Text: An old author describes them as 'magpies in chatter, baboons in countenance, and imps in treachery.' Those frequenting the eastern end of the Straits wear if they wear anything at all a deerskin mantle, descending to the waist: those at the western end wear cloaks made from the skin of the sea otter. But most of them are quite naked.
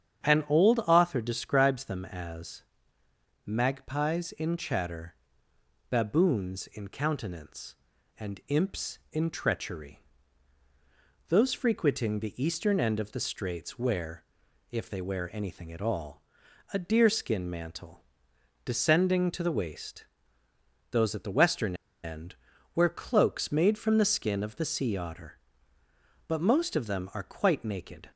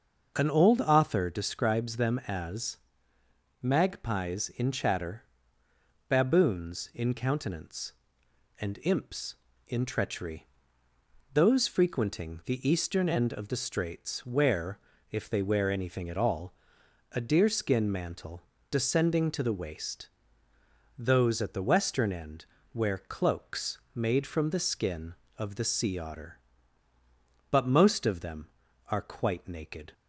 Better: second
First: starts louder than the rest; strong; until 1.3 s; 8.5 dB // pauses between "as" and "magpies"; noticeable; at 2.6 s; 0.82 s long // pauses between "wear" and "if"; noticeable; at 14.2 s; 0.48 s long // pauses between "all" and "a"; noticeable; at 16.2 s; 0.50 s long // pauses between "western" and "end"; slight; at 21.7 s; 0.29 s long // pauses between "end" and "wear"; at 22.3 s; 0.40 s long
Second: starts louder than the rest; noticeable; until 1.3 s; 6 dB // pauses between "as" and "magpies"; noticeable; at 2.7 s; 0.84 s long // pauses between "wear" and "if"; slight; at 14.7 s; 0.32 s long // pauses between "all" and "a"; noticeable; at 16.5 s; 0.60 s long // pauses between "end" and "wear"; slight; at 22.4 s; 0.26 s long

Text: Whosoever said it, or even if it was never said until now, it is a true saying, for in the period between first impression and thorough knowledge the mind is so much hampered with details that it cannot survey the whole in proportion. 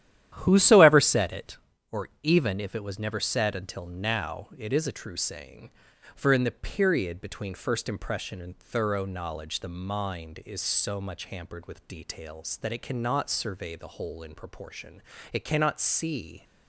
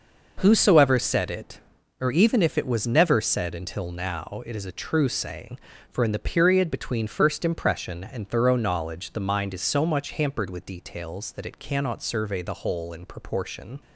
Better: second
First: starts louder than the rest; strong; until 1.3 s; 11.5 dB // goes on to say "It cannot see"; noticeable; from 15.3 s on; 1.1 s long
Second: none

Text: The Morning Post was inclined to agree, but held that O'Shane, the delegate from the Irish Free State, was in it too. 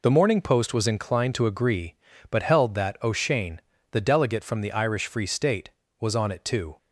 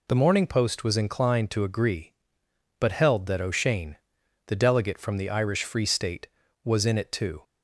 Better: second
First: says "on" for "in"; at 6.1 s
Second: none

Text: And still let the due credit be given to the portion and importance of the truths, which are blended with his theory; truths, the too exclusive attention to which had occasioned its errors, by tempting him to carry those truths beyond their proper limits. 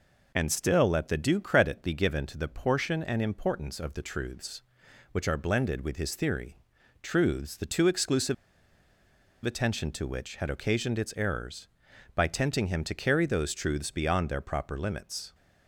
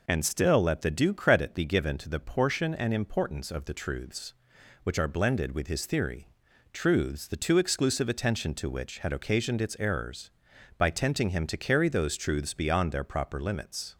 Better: second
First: pauses between "exclusive" and "attention"; at 8.3 s; 1.0 s long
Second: none

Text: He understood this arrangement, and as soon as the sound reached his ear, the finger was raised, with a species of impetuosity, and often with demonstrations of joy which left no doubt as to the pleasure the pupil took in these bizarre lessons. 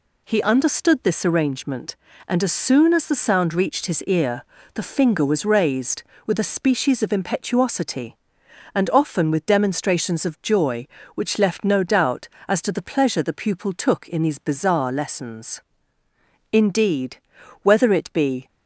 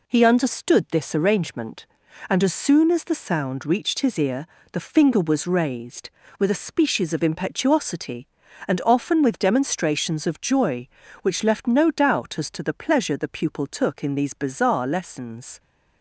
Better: second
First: goes on to say "Indeed whether it be"; strong; from 16.5 s on; 1.9 s long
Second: none

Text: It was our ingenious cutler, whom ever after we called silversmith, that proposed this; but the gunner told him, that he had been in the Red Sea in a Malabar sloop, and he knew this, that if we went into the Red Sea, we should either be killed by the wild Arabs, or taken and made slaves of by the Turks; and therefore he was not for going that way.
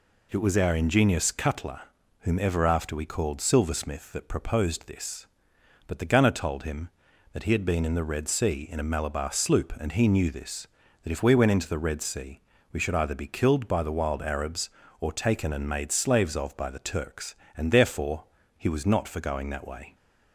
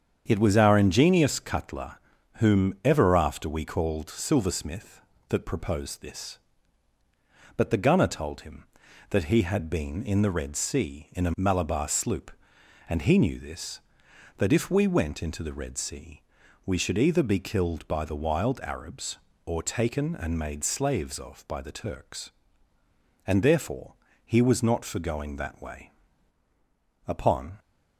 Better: first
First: pauses between "therefore" and "he"; slight; at 18.2 s; 0.34 s long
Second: starts louder than the rest; strong; until 1.2 s; 7.5 dB // pauses between "therefore" and "he"; slight; at 23.9 s; 0.30 s long // goes on to say "Upon"; from 27.0 s on; 0.52 s long

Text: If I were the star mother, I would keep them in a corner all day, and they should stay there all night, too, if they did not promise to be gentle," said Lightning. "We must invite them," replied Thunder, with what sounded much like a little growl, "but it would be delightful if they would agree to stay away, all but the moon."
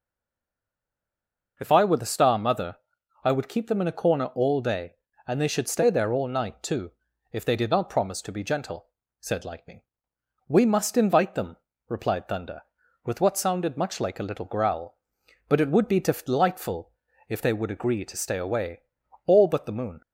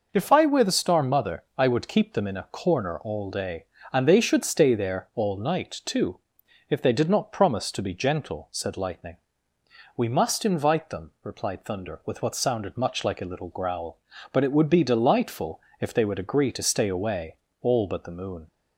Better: second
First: stays silent before the first word; noticeable; until 1.5 s; 1.5 s long // pauses between "delightful" and "if"; at 16.9 s; 0.38 s long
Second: pauses between "delightful" and "if"; slight; at 15.6 s; 0.18 s long

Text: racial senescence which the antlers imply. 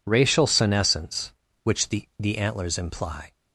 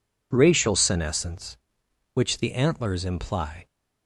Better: second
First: says "the" twice; at 2.1 s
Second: none

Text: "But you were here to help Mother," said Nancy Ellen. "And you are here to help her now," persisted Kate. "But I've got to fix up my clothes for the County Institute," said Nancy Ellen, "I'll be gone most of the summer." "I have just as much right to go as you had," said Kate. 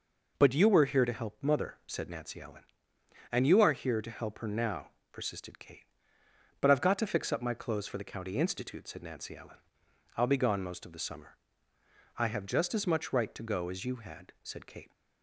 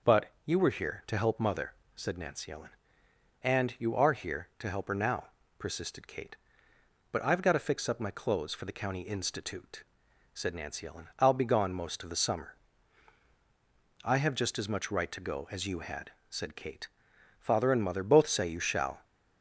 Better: first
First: none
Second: goes on to say "Father and Mother both say you shall"; from 17.3 s on; 1.6 s long

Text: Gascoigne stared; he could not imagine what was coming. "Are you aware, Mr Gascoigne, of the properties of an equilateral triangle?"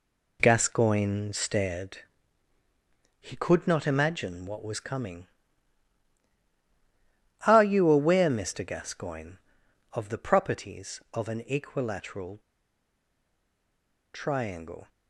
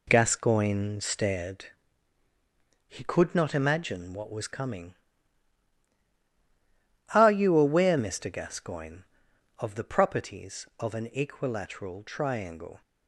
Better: second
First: pauses between "equilateral" and "triangle"; strong; at 12.3 s; 1.7 s long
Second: none

